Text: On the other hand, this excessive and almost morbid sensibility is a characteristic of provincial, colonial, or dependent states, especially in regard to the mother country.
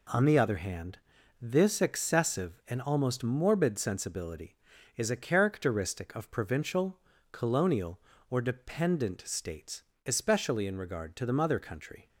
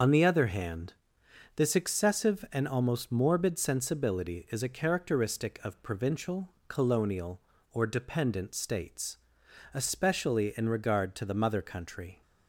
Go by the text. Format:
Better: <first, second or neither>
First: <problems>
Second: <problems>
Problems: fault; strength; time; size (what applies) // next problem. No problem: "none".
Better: first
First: none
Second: loses the start of "On"; at 0.0 s; 85 ms // starts louder than the rest; noticeable; until 1.6 s; 6 dB